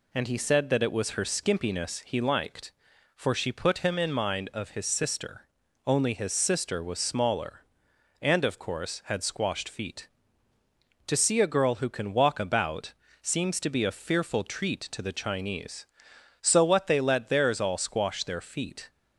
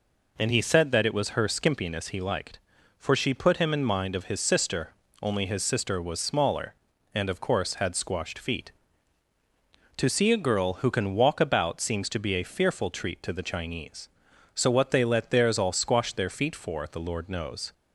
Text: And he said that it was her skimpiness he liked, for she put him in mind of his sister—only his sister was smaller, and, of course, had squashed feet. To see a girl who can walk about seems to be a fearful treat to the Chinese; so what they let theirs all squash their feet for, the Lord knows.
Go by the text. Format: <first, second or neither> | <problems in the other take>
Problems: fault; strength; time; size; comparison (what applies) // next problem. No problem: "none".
second | pauses between "about" and "seems"; slight; at 12.9 s; 0.28 s long // stops before "for the Lord knows"; at 18.8 s